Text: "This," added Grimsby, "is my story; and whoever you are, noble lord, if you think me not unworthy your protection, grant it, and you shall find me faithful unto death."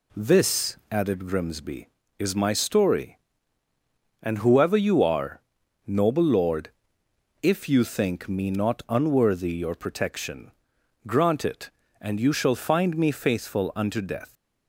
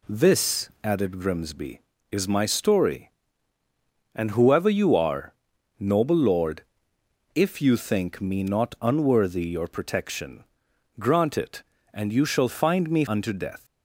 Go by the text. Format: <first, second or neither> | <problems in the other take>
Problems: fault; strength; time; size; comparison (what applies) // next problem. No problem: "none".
first | skips "faithful"; at 13.0 s